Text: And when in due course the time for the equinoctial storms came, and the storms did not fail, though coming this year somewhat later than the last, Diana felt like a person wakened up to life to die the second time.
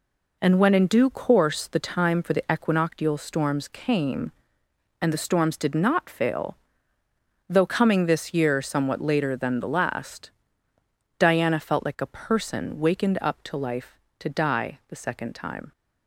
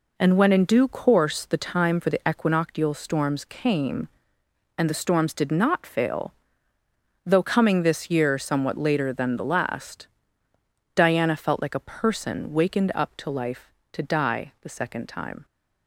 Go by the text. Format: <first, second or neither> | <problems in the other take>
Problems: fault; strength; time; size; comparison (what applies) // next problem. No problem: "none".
neither | none